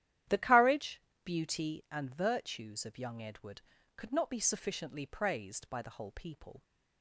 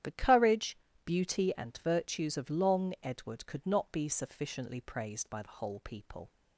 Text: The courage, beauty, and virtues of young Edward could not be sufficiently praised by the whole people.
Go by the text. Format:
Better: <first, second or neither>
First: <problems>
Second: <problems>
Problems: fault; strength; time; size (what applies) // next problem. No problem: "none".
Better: first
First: starts louder than the rest; strong; until 1.5 s; 11.5 dB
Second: starts louder than the rest; strong; until 1.2 s; 11 dB // says "long" for "young"; at 2.4 s